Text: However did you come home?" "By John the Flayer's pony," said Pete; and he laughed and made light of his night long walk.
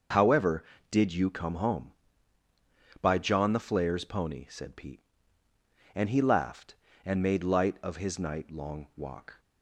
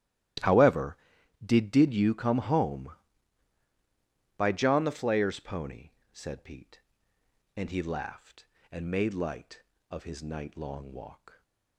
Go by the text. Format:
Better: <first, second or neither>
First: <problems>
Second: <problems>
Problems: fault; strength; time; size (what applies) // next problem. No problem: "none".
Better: first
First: none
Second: starts louder than the rest; strong; until 1.9 s; 14.5 dB // says "did" twice; at 1.7 s